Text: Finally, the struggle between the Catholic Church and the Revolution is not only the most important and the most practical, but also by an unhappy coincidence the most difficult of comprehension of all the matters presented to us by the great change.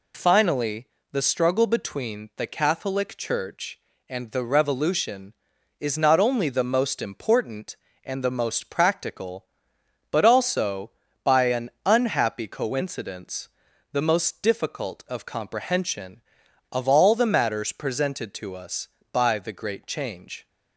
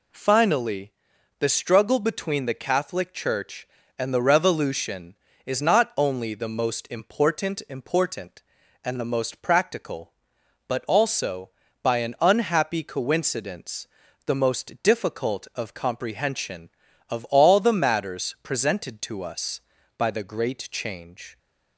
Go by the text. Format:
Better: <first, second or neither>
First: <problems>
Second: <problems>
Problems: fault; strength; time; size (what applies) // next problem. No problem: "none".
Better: first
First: pauses between "coincidence" and "the"; at 13.4 s; 0.42 s long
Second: says "important" twice; at 7.6 s // pauses between "coincidence" and "the"; at 13.8 s; 0.40 s long